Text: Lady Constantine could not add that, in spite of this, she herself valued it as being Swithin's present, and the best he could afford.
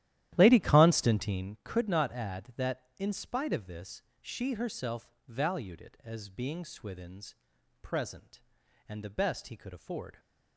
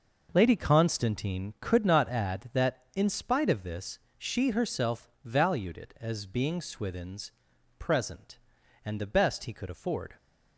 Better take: second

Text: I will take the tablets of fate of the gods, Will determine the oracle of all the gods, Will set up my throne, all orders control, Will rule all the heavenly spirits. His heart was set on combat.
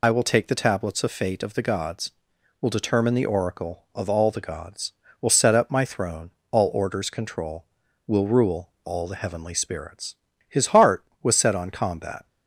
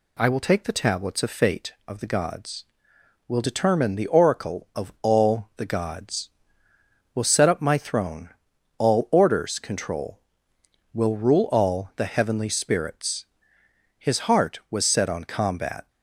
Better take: second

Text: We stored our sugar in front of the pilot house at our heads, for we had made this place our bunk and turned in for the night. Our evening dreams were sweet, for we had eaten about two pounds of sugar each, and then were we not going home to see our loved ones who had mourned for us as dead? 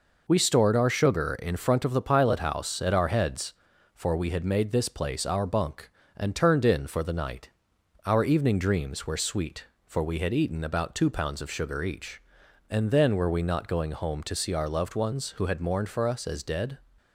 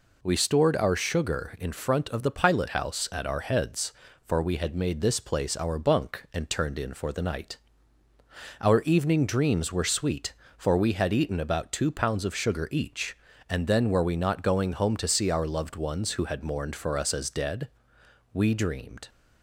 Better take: first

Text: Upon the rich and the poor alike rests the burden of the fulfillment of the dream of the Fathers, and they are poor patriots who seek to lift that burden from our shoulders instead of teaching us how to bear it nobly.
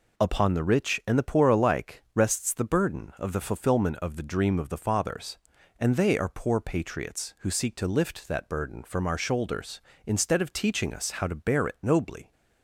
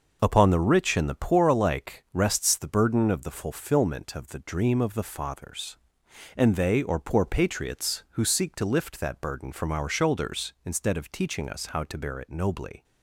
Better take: first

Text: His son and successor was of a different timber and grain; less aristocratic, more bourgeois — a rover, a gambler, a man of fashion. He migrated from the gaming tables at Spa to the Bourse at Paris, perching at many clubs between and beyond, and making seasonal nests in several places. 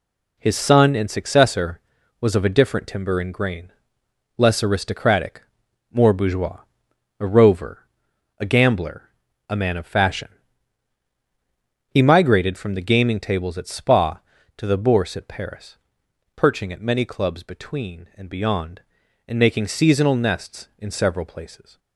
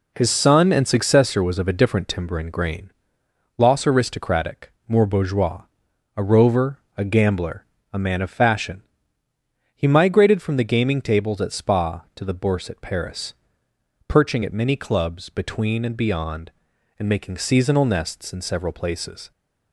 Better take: first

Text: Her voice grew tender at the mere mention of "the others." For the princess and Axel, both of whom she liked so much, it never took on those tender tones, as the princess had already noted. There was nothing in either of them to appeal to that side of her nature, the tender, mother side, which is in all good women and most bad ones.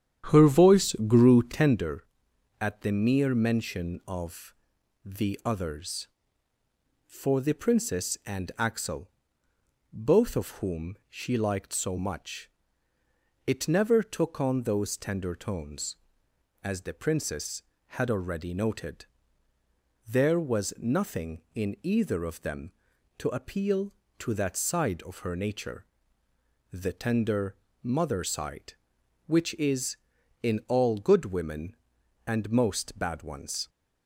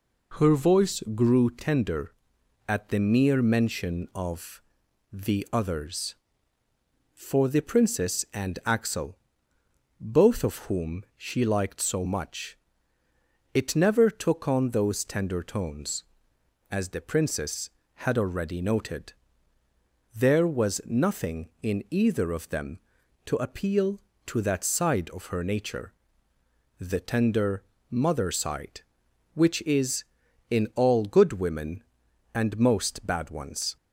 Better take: second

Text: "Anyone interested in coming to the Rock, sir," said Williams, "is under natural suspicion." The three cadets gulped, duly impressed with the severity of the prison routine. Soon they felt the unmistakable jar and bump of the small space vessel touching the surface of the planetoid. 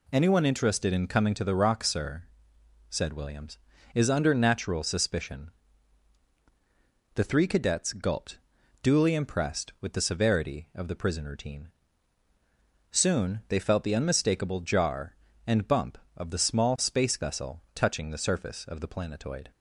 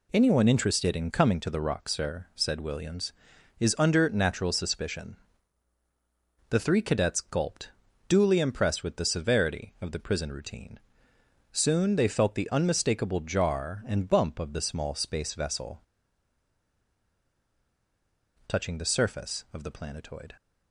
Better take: first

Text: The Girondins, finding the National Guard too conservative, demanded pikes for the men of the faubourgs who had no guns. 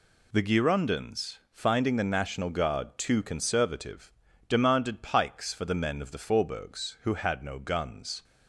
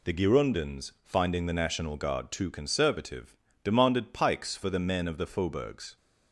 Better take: first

